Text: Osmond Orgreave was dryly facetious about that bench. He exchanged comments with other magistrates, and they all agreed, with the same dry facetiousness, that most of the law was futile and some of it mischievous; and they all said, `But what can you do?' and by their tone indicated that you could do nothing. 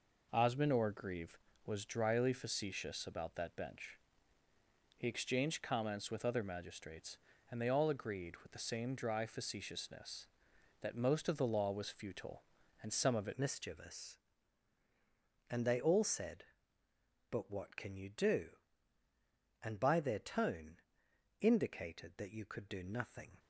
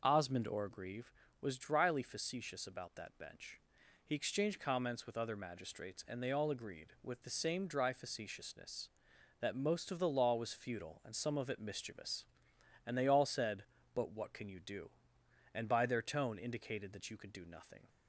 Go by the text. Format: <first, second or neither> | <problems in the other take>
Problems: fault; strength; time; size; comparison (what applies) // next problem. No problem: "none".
second | changes voice at "mischievous"; from 13.3 s on; 10.0 s long // pauses between "tone" and "indicated"; noticeable; at 20.7 s; 0.62 s long